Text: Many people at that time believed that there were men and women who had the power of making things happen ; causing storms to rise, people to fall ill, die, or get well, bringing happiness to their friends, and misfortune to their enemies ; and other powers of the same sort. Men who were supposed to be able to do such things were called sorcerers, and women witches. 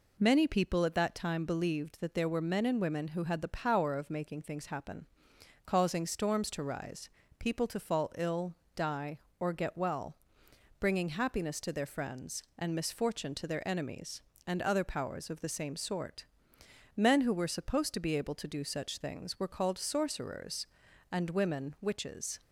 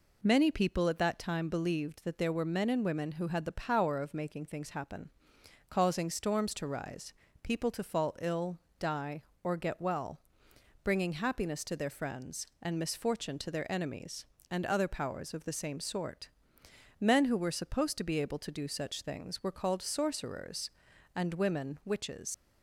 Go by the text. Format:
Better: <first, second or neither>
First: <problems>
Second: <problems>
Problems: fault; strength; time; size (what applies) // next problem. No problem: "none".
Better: first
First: none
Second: leaves "witches" unfinished; at 22.3 s; 95 ms